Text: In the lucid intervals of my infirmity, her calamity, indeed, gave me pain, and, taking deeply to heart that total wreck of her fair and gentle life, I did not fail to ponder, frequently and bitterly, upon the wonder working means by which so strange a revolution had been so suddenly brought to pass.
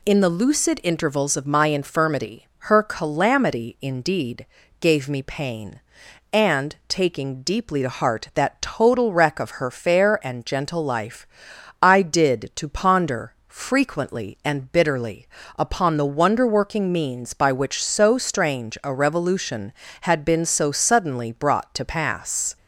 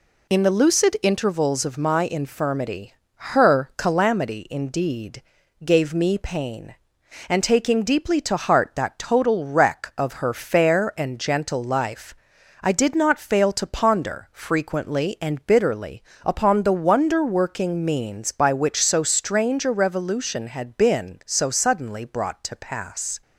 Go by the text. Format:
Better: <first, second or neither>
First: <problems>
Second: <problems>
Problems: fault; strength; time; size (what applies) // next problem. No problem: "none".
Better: second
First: skips "not fail"; at 12.5 s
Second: none